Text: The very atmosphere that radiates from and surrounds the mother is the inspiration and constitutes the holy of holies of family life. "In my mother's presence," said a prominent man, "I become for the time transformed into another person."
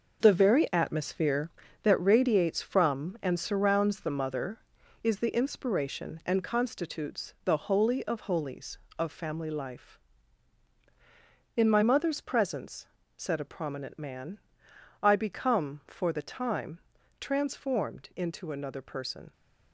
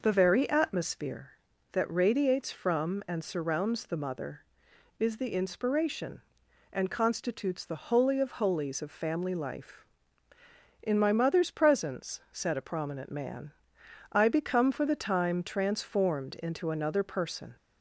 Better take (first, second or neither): second